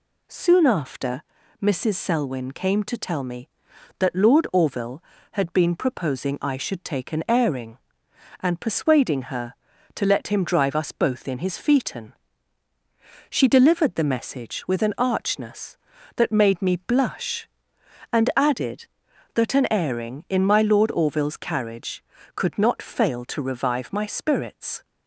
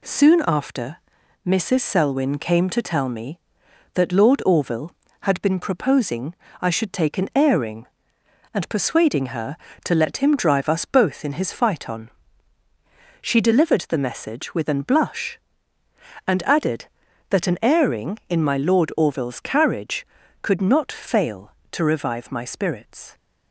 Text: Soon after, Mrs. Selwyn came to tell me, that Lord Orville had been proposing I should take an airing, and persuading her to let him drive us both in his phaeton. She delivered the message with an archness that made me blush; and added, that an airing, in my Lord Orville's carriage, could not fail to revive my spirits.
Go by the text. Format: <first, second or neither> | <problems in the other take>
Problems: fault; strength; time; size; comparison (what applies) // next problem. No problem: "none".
first | pauses between "proposing" and "I"; slight; at 6.3 s; 0.24 s long // skips "archness that made me"; at 14.8 s